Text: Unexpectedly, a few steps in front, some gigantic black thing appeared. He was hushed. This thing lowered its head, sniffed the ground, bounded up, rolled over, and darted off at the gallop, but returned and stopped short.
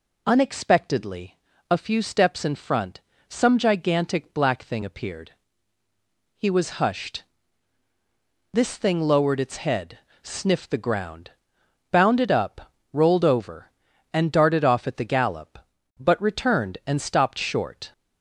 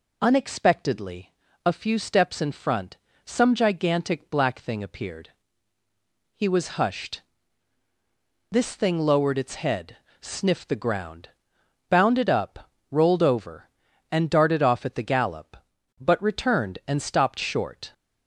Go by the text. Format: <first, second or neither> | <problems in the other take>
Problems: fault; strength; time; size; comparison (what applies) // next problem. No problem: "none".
neither | none